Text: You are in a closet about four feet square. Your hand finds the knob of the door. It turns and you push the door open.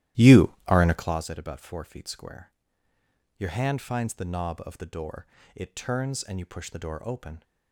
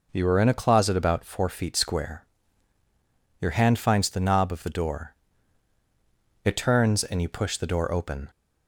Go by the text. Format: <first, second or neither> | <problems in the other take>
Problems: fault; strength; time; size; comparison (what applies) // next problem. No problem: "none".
second | starts louder than the rest; strong; until 1.2 s; 13.5 dB